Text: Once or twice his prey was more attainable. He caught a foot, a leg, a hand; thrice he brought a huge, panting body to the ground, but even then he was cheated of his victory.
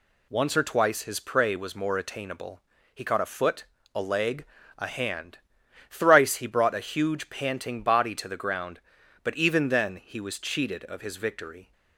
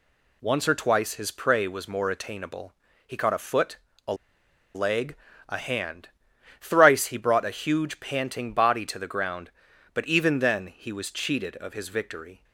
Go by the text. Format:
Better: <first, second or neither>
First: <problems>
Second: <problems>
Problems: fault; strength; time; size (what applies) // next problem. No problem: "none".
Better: first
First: none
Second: pauses between "a" and "leg"; noticeable; at 4.1 s; 0.61 s long